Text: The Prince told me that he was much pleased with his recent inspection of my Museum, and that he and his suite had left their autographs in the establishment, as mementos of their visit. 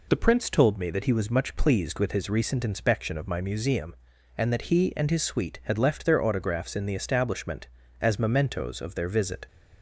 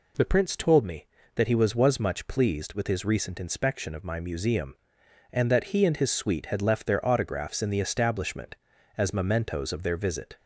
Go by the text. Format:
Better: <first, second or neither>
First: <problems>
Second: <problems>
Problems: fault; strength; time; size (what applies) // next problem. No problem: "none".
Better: first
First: none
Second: says "was" twice; at 1.7 s